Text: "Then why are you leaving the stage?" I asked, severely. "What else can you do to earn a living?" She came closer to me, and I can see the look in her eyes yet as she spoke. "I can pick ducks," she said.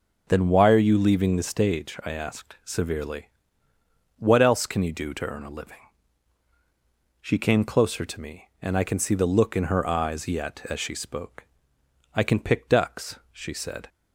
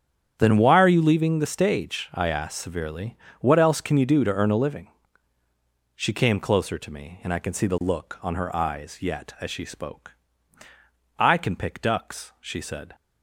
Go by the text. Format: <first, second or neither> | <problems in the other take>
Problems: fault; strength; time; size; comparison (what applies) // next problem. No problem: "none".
first | starts louder than the rest; strong; until 1.3 s; 8.5 dB // says "on" for "in"; at 8.2 s